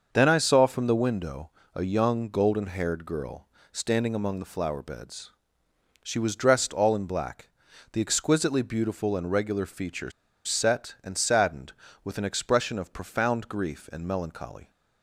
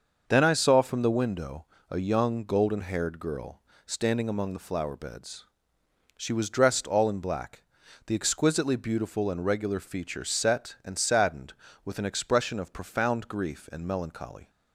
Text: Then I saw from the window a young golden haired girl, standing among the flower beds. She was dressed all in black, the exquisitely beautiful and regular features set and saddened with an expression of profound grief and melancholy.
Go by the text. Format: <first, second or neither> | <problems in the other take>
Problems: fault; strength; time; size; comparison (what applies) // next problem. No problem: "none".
second | starts louder than the rest; until 1.1 s; 6.5 dB; also in the second // pauses between "window" and "a"; slight; at 1.5 s; 0.24 s long; slight in the second // pauses between "features" and "set"; at 10.1 s; 0.36 s long